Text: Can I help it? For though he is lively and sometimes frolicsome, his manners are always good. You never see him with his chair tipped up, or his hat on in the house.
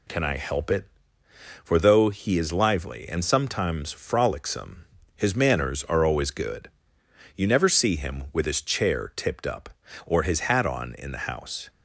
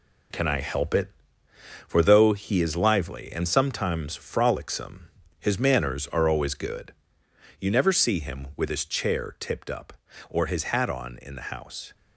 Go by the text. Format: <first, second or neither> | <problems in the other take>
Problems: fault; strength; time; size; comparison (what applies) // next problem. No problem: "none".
first | gets quieter; throughout; 6.5 dB